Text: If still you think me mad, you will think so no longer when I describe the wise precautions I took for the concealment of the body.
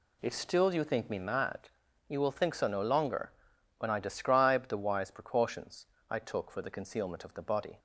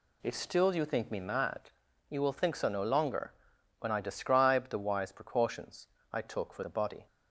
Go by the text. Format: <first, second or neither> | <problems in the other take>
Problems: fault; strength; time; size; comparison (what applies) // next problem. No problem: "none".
first | pauses between "longer" and "when"; noticeable; at 3.3 s; 0.46 s long; noticeable in the first // pauses between "precautions" and "I"; slight; at 5.8 s; 0.26 s long; slight in the first // skips "the concealment of"; at 6.6 s